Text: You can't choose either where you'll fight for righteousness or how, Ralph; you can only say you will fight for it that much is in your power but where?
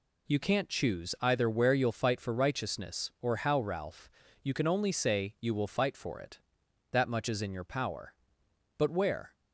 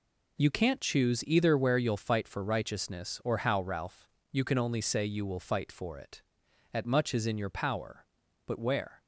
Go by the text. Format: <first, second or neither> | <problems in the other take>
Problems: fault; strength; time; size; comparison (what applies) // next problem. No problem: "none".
first | says "at" for "that"; at 6.7 s